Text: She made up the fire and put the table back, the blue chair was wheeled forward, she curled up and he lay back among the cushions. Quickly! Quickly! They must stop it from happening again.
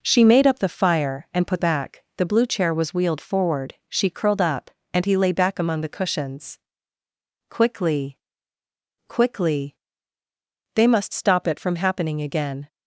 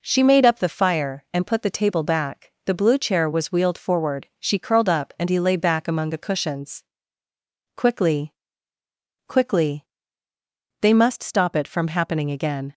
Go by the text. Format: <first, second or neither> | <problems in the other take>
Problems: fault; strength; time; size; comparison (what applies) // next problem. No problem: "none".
second | skips "the table"; at 1.6 s